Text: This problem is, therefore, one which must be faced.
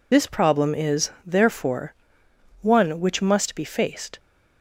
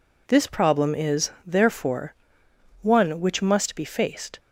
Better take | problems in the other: second | loses the start of "This"; at 0.1 s; 45 ms

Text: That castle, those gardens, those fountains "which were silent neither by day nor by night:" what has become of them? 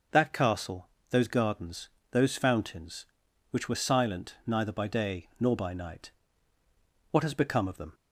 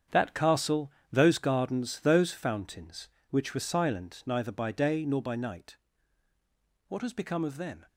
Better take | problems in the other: first | gets quieter; strong; throughout; 11 dB

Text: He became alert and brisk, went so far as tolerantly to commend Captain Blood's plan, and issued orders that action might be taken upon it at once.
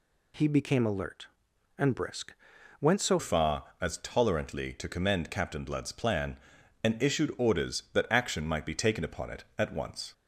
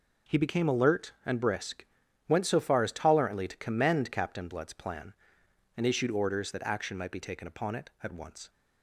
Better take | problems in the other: second | changes voice at "far"; from 3.1 s on; 7.0 s long

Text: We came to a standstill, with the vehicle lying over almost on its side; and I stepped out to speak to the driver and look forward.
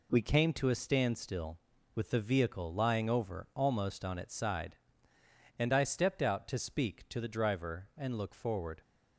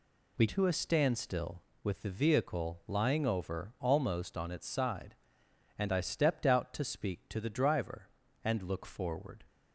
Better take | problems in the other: first | skips "came"; at 0.4 s

